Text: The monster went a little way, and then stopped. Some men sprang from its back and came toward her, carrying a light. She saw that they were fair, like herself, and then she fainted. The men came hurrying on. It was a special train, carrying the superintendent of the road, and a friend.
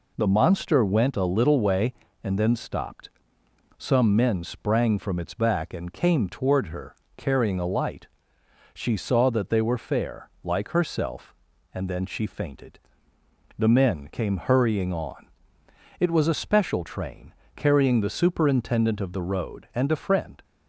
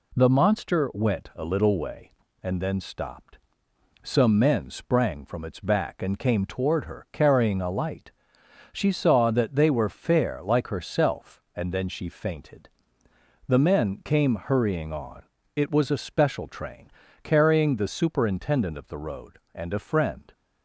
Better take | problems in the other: neither | none

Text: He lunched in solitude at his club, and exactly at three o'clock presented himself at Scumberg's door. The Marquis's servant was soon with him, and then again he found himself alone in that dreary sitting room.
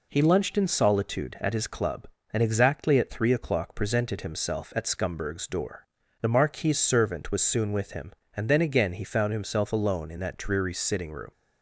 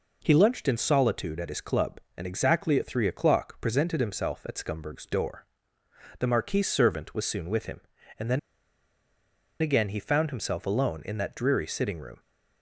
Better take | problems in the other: first | pauses between "then" and "again"; at 8.3 s; 1.2 s long

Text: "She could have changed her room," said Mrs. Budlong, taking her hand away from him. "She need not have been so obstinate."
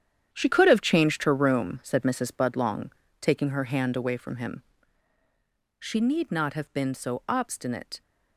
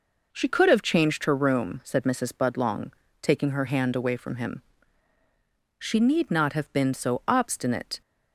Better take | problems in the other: second | gets quieter; strong; throughout; 12 dB

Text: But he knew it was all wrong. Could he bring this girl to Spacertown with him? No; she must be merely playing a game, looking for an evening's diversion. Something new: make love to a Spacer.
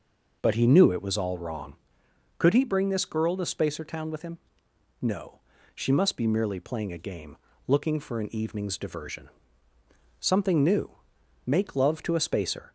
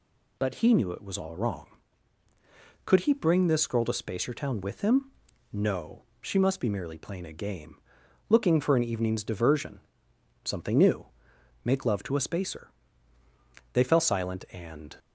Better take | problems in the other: first | goes on to say "They fell silent and"; noticeable; from 13.7 s on; 1.2 s long

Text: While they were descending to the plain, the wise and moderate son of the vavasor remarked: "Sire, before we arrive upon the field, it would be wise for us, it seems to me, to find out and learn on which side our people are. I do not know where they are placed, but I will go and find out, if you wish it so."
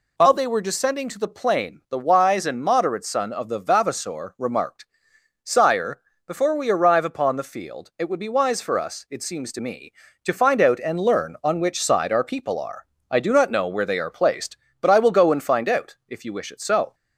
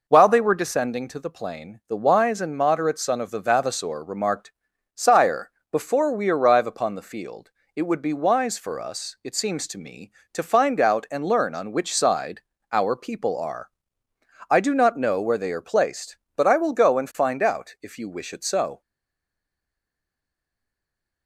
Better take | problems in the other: first | pauses between "side" and "our"; slight; at 12.3 s; 0.32 s long // stays silent after the last word; from 18.8 s on; 2.4 s long

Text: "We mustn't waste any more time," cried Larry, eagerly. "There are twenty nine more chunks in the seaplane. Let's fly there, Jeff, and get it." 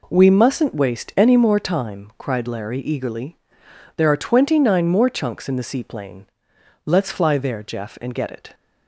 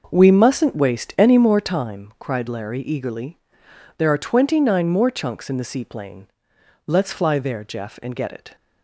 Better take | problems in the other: first | starts louder than the rest; noticeable; until 1.8 s; 5.5 dB

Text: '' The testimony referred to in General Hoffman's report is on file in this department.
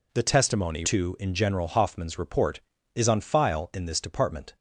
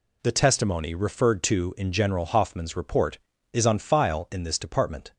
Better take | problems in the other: second | skips "referred"; at 0.8 s

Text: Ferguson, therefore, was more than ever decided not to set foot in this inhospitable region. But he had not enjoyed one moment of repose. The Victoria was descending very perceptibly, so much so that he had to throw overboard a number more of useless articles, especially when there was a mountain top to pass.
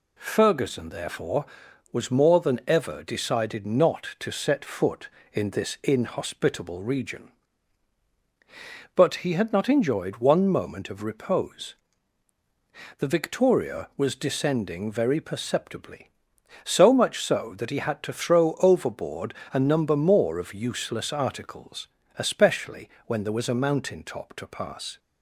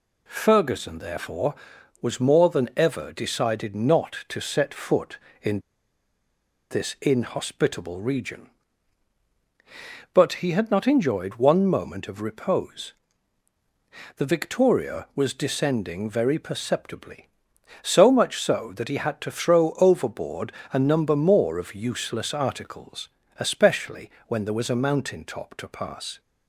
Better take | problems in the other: first | pauses between "in" and "this"; at 5.6 s; 1.0 s long // pauses between "overboard" and "a"; slight; at 20.5 s; 0.20 s long; slight in the first // pauses between "especially" and "when"; slight; at 24.0 s; 0.18 s long; slight in the first

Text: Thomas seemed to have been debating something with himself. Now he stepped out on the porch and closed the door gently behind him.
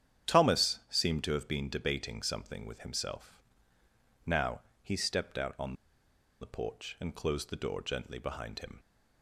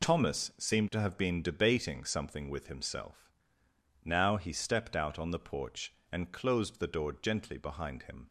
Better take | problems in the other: second | starts louder than the rest; strong; until 1.3 s; 9 dB // pauses between "Now" and "he"; slight; at 4.6 s; 0.22 s long // pauses between "on" and "the"; noticeable; at 5.7 s; 0.67 s long

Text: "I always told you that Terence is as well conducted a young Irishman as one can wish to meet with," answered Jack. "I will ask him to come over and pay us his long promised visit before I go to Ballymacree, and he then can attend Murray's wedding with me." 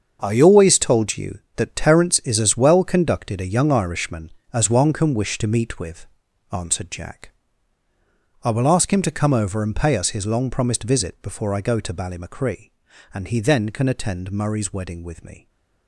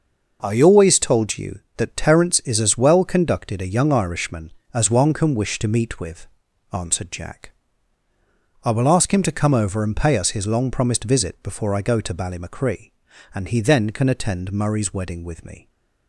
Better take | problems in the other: second | gets quieter; strong; throughout; 11 dB

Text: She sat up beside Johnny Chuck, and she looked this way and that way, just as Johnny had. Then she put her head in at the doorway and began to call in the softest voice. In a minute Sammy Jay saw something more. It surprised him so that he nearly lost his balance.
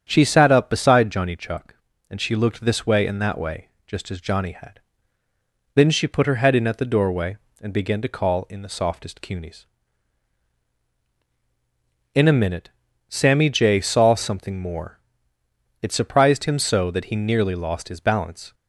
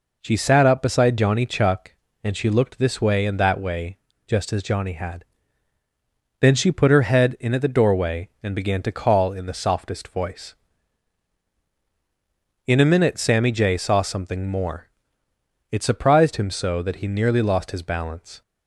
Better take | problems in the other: second | starts louder than the rest; strong; until 1.0 s; 8 dB // says "cunies" for "voice"; at 9.1 s // pauses between "minute" and "Sammy"; at 12.6 s; 0.40 s long

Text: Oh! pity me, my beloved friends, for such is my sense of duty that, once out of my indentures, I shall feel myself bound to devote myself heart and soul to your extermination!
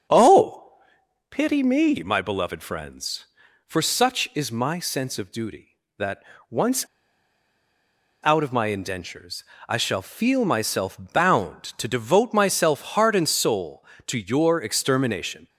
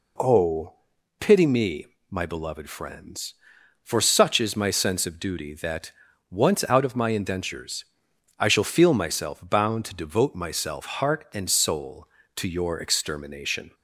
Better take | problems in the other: second | starts louder than the rest; strong; until 1.8 s; 7 dB // pauses between "once" and "out"; strong; at 6.8 s; 1.3 s long

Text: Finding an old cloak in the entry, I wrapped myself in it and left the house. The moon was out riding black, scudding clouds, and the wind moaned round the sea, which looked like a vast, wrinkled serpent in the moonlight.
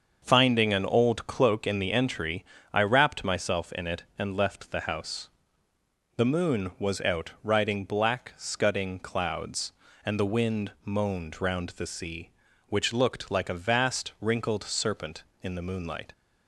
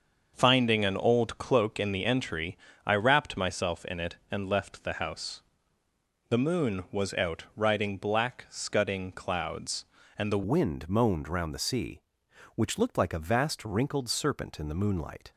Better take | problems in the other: first | starts louder than the rest; until 1.3 s; 6.5 dB; also in the first // changes voice at "wind"; from 10.4 s on; 4.9 s long

